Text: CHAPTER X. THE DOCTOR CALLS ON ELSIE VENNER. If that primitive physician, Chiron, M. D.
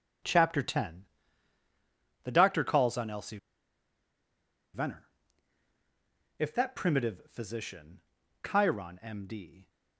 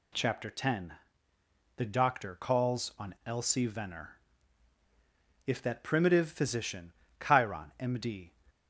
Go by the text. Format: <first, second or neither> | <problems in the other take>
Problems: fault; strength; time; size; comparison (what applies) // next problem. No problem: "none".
second | starts louder than the rest; strong; until 2.4 s; 8.5 dB // pauses between "ELSIE" and "VENNER"; strong; at 3.3 s; 1.3 s long